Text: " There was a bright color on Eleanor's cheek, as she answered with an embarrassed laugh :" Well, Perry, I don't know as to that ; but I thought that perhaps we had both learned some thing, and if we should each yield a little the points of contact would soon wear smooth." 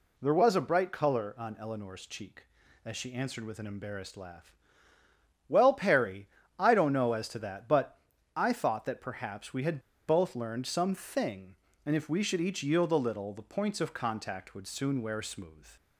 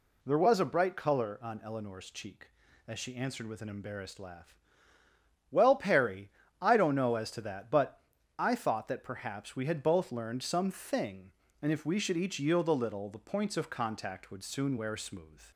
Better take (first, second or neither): second